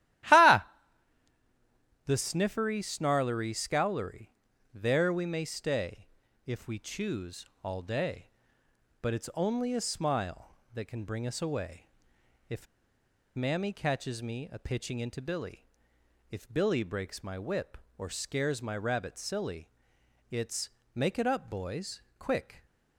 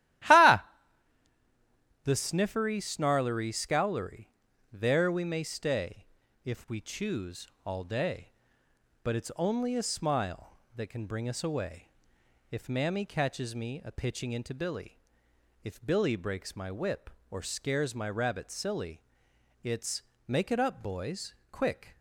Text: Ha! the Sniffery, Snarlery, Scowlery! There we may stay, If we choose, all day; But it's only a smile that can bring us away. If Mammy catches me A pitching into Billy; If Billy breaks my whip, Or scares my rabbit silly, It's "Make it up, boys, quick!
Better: second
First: starts louder than the rest; strong; until 2.6 s; 14.5 dB // pauses between "If" and "Mammy"; noticeable; at 12.6 s; 0.69 s long // pauses between "It's" and "Make"; slight; at 20.6 s; 0.24 s long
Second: starts louder than the rest; strong; until 2.6 s; 14.5 dB // pauses between "It's" and "Make"; slight; at 20.0 s; 0.24 s long

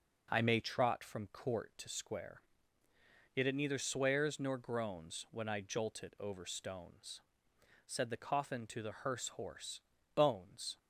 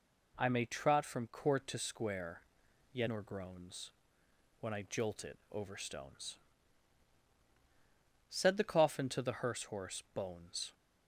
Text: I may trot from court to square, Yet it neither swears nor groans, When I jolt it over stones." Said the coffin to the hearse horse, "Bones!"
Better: first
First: none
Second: skips "it neither swears"; at 3.0 s

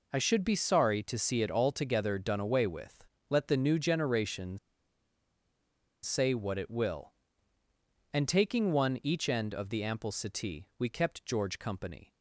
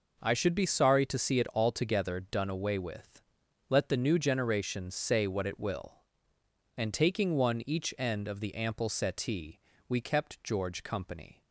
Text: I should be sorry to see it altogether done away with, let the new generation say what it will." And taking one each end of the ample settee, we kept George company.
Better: second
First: pauses between "generation" and "say"; strong; at 4.5 s; 1.4 s long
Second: none

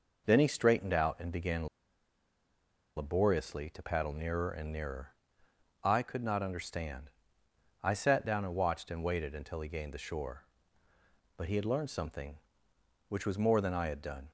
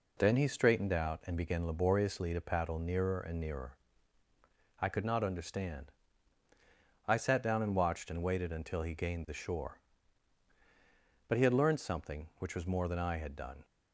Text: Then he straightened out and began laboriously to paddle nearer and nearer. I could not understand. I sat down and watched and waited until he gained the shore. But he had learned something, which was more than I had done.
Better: second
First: pauses between "began" and "laboriously"; strong; at 1.6 s; 1.2 s long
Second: none

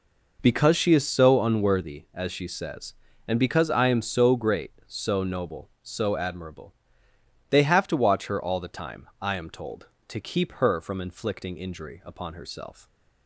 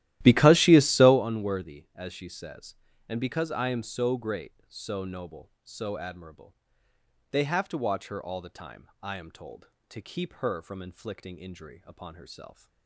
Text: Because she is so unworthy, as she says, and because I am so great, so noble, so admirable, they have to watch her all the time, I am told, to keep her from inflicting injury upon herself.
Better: first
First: none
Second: starts louder than the rest; strong; until 1.3 s; 14.5 dB

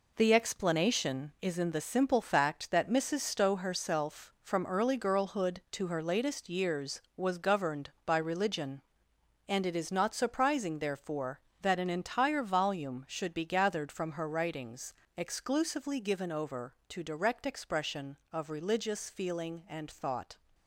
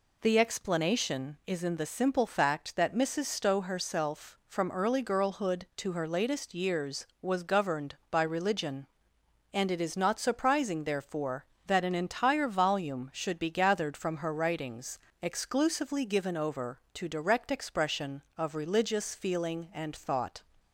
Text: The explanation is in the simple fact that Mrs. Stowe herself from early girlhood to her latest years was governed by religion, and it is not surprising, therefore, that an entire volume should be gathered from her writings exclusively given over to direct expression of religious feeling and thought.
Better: second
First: gets quieter; strong; throughout; 7.5 dB // pauses between "writings" and "exclusively"; slight; at 14.9 s; 0.24 s long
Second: pauses between "writings" and "exclusively"; slight; at 14.9 s; 0.24 s long

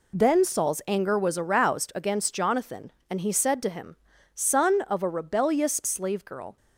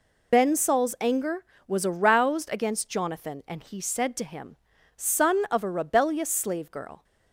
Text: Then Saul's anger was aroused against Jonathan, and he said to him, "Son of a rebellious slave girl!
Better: first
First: none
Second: loses the start of "Then"; at 0.3 s; 110 ms

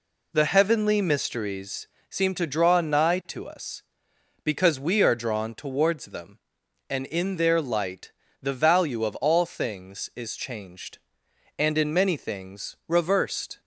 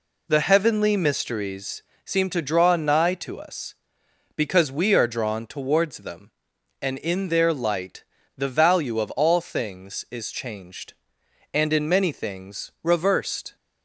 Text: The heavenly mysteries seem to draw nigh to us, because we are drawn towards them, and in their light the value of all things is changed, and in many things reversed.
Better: neither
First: pauses between "mysteries" and "seem"; slight; at 1.8 s; 0.22 s long // pauses between "light" and "the"; slight; at 8.1 s; 0.30 s long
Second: pauses between "mysteries" and "seem"; slight; at 1.8 s; 0.22 s long // pauses between "light" and "the"; slight; at 8.0 s; 0.33 s long

